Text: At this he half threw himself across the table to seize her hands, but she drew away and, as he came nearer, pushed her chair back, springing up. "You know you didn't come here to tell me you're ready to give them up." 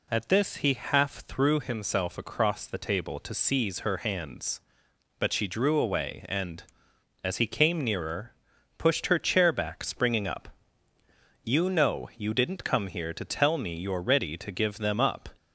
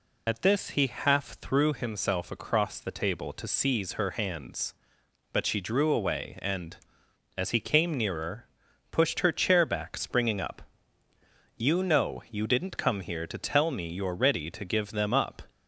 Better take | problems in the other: first | loses the start of "At"; at 0.2 s; 40 ms

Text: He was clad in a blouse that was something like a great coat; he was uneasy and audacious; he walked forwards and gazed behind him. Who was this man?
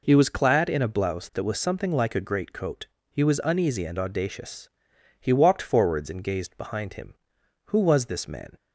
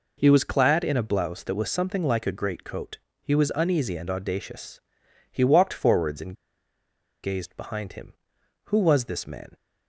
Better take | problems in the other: first | pauses between "and" and "gazed"; noticeable; at 6.3 s; 0.88 s long

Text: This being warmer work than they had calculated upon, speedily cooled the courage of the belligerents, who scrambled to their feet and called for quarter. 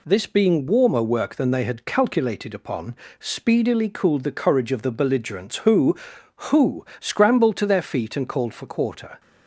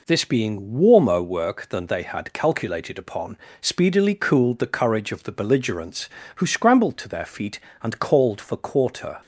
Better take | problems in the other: second | says "who" twice; at 6.3 s

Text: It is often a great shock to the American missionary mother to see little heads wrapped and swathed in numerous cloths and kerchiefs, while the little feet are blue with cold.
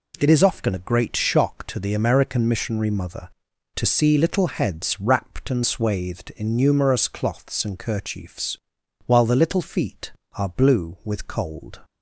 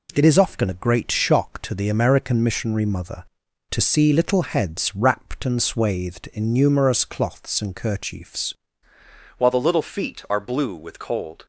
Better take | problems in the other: first | changes voice at "while"; from 9.3 s on; 2.1 s long

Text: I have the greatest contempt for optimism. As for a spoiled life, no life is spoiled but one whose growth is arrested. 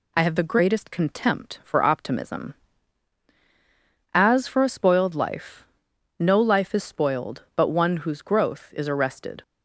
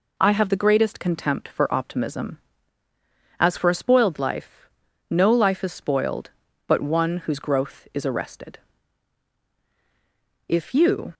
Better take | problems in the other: first | goes on to say "If you"; noticeable; from 10.4 s on; 0.66 s long

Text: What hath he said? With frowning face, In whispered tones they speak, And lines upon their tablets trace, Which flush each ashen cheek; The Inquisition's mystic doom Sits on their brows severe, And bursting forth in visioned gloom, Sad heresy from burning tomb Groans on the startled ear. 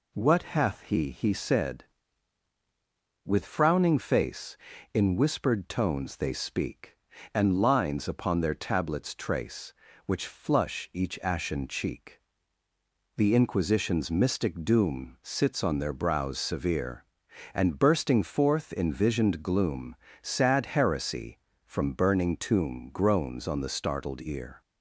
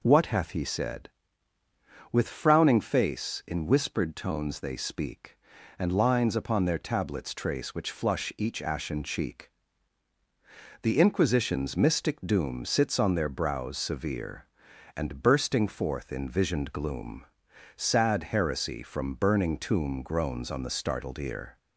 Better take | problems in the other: second | says "he" twice; at 1.0 s

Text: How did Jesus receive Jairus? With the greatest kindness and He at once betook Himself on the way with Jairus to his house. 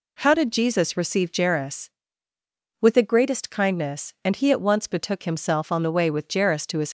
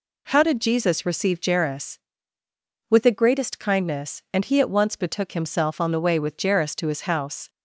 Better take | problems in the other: second | stops before "house"; at 6.8 s

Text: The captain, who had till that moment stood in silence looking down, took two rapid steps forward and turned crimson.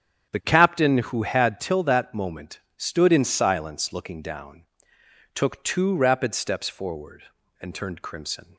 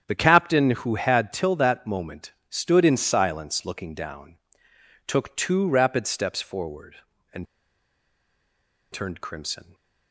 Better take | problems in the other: first | starts louder than the rest; strong; until 1.0 s; 9 dB; strong in the first // pauses between "moment" and "stood"; slight; at 2.3 s; 0.18 s long; slight in the first // pauses between "and" and "turned"; strong; at 7.4 s; 1.4 s long

